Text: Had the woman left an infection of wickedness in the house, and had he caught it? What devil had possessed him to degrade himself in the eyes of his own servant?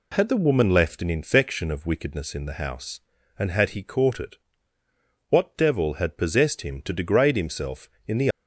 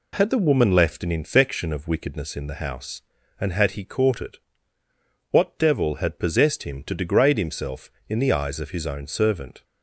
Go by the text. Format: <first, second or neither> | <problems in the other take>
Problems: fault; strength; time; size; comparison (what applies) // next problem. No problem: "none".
second | stops before "eyes of his own servant"; at 8.3 s